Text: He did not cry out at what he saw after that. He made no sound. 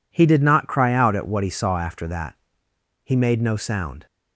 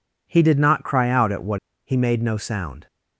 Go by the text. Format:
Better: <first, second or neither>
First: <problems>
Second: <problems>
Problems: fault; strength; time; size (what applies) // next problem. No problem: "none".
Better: first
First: none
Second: skips "he saw after that"; at 1.7 s